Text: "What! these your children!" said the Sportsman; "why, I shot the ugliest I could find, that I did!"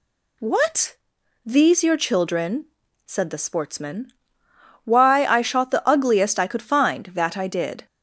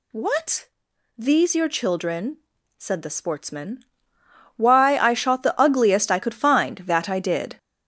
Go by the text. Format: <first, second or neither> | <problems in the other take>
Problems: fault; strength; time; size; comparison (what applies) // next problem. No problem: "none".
first | gets louder; throughout; 6.5 dB